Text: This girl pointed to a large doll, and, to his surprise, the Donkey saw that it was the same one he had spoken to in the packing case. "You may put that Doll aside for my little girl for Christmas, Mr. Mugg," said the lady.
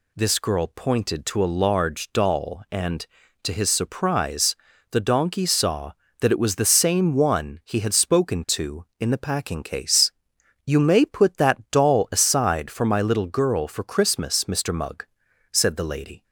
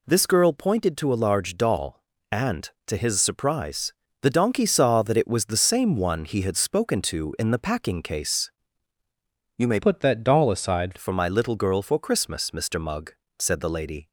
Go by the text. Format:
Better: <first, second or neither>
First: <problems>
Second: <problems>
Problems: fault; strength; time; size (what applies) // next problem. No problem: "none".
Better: first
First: none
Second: changes voice from "put" to "aside"; from 9.8 to 10.9 s; 1.1 s long